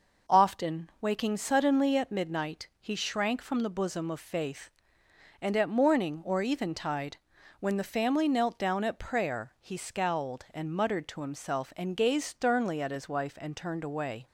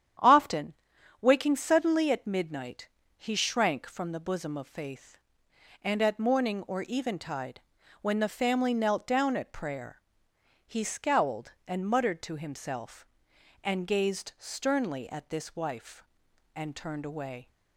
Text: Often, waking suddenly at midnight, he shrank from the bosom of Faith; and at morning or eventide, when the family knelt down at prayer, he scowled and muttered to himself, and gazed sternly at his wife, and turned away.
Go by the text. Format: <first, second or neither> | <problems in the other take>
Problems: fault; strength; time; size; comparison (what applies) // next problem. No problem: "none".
first | starts louder than the rest; strong; until 1.6 s; 9.5 dB // says "this" for "his"; at 15.2 s